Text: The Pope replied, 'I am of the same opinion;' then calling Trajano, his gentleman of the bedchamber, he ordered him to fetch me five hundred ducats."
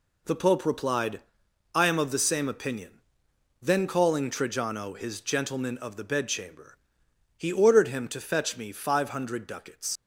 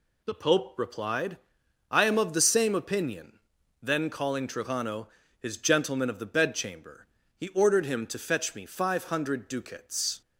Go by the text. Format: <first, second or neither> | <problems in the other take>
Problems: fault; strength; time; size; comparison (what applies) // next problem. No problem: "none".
second | leaves "ducats" unfinished; at 9.9 s; 90 ms